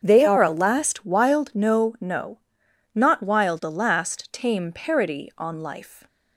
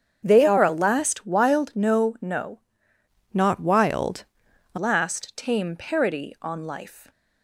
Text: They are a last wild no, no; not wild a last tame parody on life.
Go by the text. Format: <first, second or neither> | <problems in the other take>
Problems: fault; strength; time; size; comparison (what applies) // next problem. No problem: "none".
first | starts louder than the rest; strong; until 1.2 s; 8 dB; strong in the first // changes voice from "not" to "a"; from 3.3 to 4.7 s; 1.4 s long // pauses between "wild" and "a"; noticeable; at 4.2 s; 0.48 s long